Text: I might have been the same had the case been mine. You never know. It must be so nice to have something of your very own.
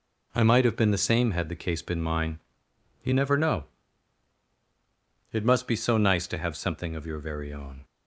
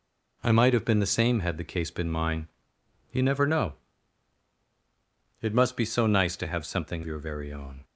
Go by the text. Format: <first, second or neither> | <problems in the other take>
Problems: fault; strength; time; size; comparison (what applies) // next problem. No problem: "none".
first | skips "of"; at 7.0 s